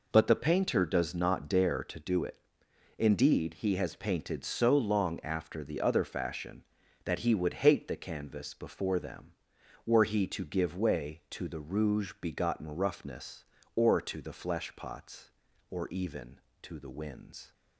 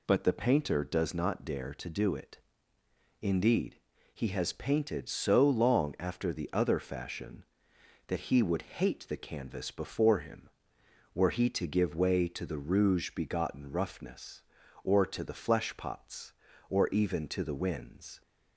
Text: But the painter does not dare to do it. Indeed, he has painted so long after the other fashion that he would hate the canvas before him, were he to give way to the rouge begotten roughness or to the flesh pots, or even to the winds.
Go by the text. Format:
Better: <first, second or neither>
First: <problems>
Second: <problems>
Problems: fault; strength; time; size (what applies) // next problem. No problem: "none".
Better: second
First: says "them" for "him"; at 8.9 s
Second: none